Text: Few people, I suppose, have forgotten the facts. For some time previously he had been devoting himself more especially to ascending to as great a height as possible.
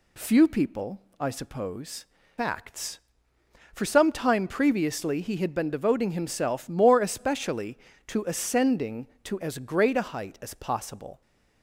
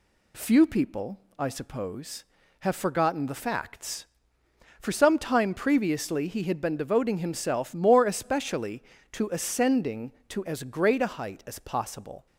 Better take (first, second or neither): second